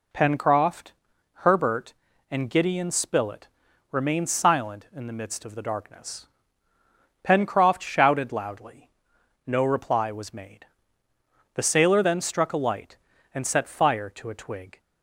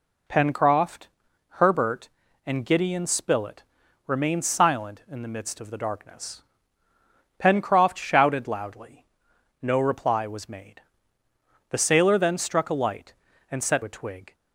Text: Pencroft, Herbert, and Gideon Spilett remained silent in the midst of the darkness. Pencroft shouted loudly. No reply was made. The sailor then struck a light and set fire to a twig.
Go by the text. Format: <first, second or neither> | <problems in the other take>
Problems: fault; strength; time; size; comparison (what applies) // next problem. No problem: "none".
first | pauses between "Spilett" and "remained"; at 3.6 s; 0.44 s long; also in the first // skips "fire to"; at 13.8 s